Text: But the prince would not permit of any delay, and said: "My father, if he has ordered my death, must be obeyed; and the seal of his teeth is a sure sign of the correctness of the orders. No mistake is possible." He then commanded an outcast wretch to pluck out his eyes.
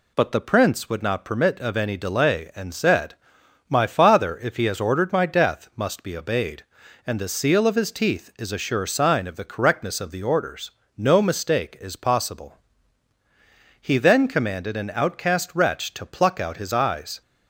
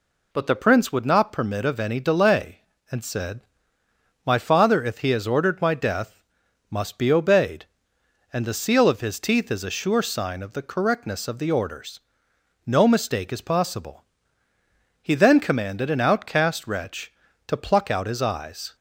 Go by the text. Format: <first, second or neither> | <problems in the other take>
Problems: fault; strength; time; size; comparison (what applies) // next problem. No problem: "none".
neither | none